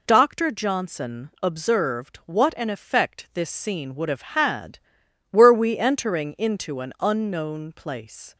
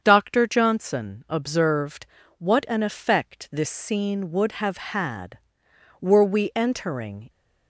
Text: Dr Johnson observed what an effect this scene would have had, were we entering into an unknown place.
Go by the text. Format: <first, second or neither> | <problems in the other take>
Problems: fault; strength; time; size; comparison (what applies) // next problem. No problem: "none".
first | starts louder than the rest; strong; until 1.0 s; 7.5 dB // pauses between "observed" and "what"; slight; at 2.0 s; 0.32 s long // stops before "into an unknown place"; at 7.2 s